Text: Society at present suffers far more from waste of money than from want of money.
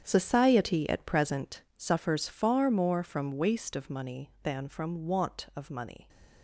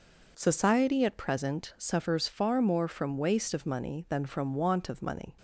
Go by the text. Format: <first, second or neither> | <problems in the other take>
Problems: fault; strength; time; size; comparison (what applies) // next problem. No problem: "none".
second | gets quieter; strong; throughout; 12 dB